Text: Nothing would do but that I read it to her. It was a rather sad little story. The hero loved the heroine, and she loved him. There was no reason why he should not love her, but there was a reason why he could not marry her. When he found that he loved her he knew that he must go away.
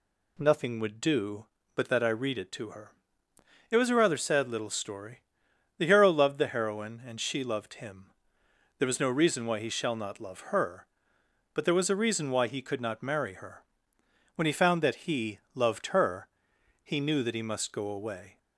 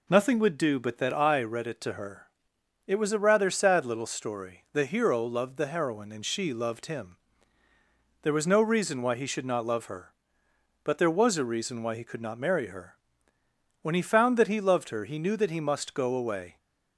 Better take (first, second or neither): second